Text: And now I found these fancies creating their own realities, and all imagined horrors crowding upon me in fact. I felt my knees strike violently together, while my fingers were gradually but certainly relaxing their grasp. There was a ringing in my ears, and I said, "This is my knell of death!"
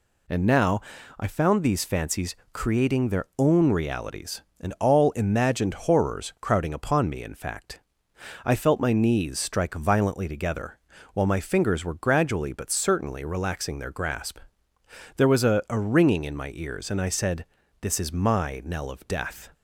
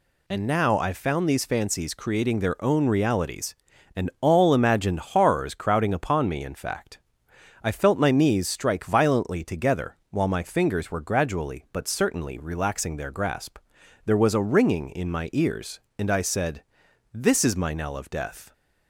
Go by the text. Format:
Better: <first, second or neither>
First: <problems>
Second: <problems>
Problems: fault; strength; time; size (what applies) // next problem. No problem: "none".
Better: second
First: pauses between "now" and "I"; at 0.8 s; 0.38 s long // pauses between "fancies" and "creating"; slight; at 2.3 s; 0.18 s long // says "a" twice; at 15.6 s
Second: none